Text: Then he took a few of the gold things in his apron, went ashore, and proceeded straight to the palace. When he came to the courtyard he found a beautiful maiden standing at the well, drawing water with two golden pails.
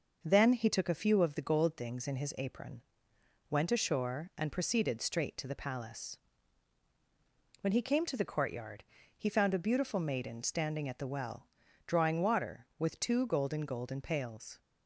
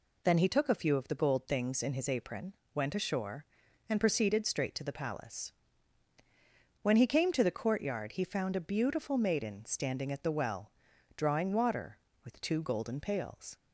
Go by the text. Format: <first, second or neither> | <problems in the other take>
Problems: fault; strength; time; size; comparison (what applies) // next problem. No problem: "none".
second | pauses between "courtyard" and "he"; slight; at 8.8 s; 0.34 s long // says "golden" twice; at 13.6 s